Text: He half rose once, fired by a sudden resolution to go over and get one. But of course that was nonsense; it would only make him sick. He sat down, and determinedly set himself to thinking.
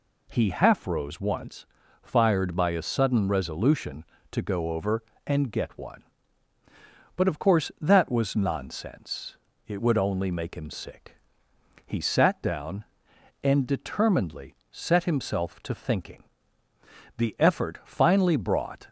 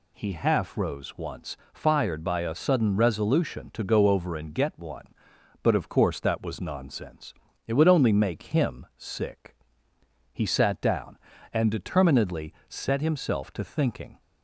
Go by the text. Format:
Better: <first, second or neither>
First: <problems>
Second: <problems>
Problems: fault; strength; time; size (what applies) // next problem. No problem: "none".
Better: second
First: pauses between "determinedly" and "set"; slight; at 14.5 s; 0.16 s long // goes on to say "The effort finally brought"; strong; from 17.1 s on; 1.7 s long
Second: none